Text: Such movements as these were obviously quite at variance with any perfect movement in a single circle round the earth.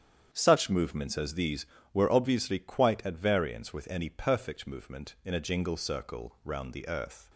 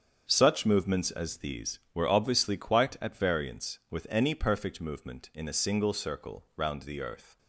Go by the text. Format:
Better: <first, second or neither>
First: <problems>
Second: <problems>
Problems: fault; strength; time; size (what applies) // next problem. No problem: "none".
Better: second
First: starts louder than the rest; strong; until 1.3 s; 8.5 dB // says "jingle" for "single"; at 5.4 s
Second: starts louder than the rest; strong; until 1.3 s; 7.5 dB